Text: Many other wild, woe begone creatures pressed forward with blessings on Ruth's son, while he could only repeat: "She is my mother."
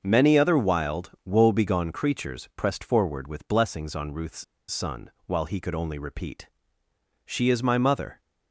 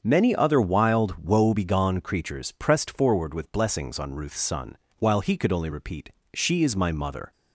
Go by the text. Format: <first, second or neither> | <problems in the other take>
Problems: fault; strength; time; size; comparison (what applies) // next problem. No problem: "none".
second | starts louder than the rest; until 1.0 s; 6.5 dB; also in the second // pauses between "Ruth's" and "son"; slight; at 4.4 s; 0.26 s long